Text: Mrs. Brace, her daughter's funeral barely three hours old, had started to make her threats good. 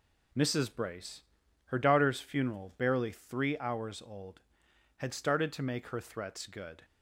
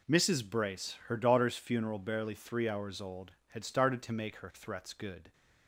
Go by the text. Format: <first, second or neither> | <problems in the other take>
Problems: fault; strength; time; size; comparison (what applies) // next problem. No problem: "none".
neither | none